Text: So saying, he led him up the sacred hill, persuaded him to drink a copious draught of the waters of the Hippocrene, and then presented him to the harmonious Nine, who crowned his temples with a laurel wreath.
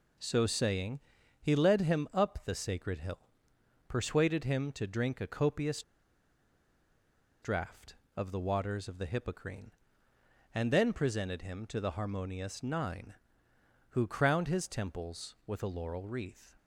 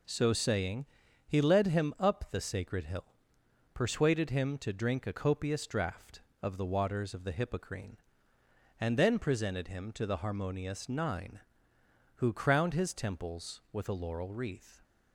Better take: second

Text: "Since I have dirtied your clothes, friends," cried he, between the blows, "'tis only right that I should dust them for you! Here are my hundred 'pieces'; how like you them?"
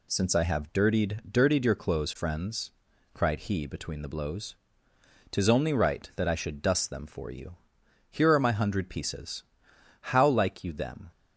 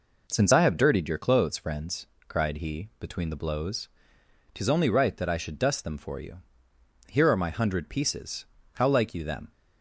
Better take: second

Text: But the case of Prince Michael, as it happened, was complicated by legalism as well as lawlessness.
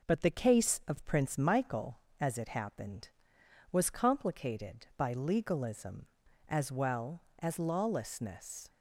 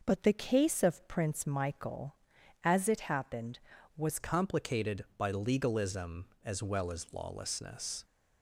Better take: first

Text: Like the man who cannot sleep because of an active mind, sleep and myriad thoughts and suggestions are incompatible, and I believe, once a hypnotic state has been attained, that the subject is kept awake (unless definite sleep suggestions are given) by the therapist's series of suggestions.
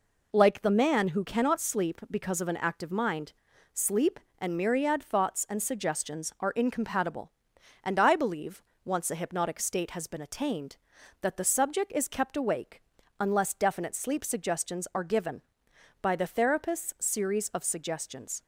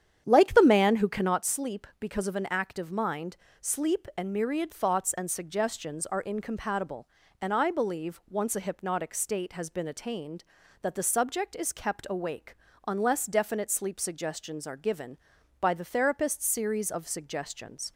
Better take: first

